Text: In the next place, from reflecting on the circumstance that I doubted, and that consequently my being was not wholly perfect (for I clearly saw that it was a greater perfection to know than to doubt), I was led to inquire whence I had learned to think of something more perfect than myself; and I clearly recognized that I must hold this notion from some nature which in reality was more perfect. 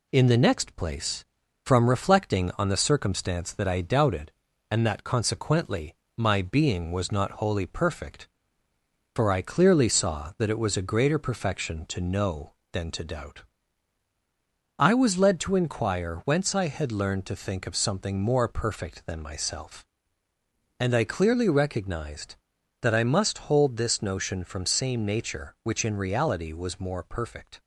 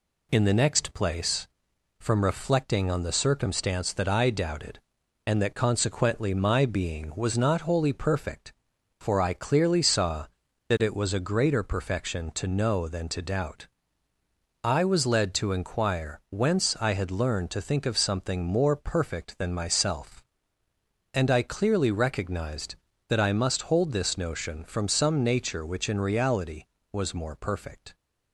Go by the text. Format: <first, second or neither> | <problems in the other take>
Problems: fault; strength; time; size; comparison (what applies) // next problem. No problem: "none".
second | pauses between "consequently" and "my"; slight; at 5.9 s; 0.22 s long // says "same" for "some"; at 24.6 s